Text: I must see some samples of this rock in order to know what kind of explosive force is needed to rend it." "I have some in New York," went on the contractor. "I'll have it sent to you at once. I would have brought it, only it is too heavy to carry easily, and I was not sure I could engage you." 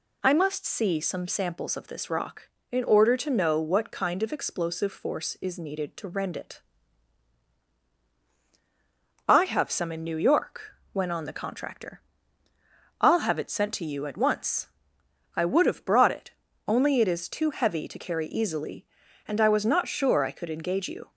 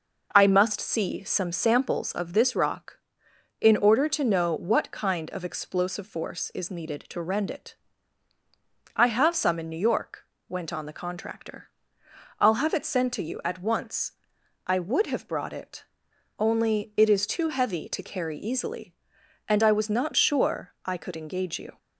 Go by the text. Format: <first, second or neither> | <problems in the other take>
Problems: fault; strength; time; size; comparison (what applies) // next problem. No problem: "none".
neither | none